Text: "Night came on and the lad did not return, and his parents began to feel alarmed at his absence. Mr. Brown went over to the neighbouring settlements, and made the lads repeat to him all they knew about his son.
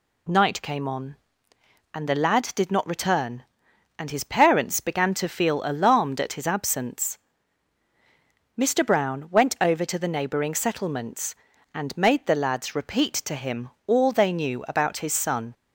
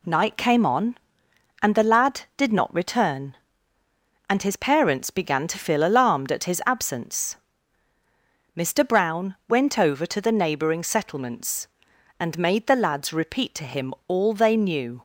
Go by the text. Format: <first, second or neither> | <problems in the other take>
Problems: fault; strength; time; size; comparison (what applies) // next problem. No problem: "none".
first | pauses between "him" and "all"; slight; at 13.9 s; 0.16 s long; slight in the first // stops before "about his son"; at 14.9 s